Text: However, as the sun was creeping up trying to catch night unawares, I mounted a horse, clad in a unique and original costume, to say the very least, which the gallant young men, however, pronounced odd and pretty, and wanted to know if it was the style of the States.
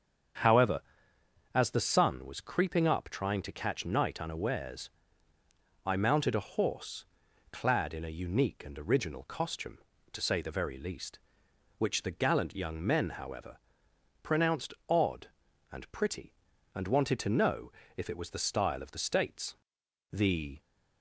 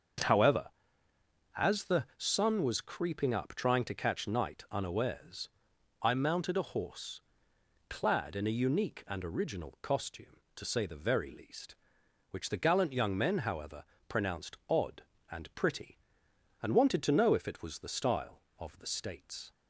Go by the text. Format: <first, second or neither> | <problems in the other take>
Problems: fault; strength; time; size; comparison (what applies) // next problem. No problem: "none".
second | starts louder than the rest; strong; until 2.1 s; 7.5 dB; also in the second // pauses between "pronounced" and "odd"; slight; at 14.7 s; 0.16 s long // pauses between "know" and "if"; slight; at 17.7 s; 0.24 s long // goes on to say "The"; slight; from 20.1 s on; 0.48 s long